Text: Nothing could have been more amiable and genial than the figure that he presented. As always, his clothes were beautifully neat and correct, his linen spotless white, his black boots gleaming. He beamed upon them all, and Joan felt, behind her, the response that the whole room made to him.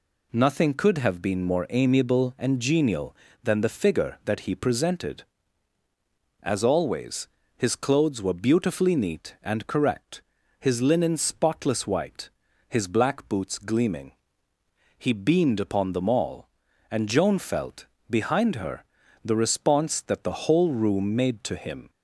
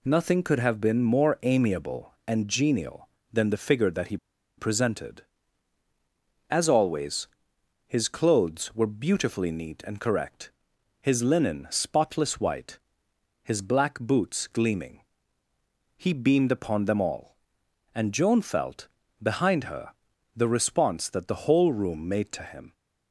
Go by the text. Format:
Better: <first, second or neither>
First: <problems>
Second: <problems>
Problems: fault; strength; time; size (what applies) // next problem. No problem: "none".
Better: first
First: none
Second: pauses between "he" and "presented"; at 4.1 s; 0.41 s long